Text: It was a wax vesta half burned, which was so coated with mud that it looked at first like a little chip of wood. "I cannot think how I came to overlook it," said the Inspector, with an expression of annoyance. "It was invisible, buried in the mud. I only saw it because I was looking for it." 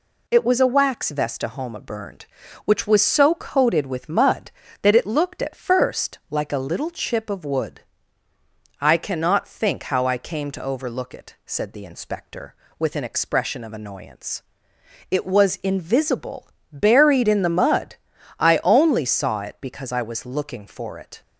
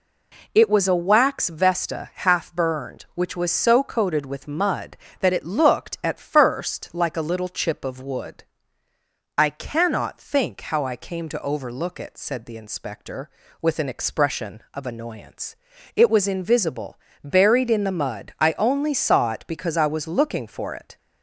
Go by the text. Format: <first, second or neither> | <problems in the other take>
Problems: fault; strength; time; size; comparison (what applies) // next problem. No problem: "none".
second | says "homa" for "half"; at 1.4 s